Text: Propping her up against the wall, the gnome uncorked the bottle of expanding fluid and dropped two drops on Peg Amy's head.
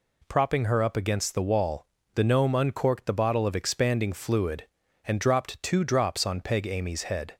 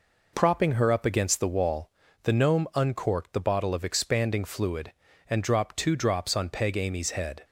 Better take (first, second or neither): neither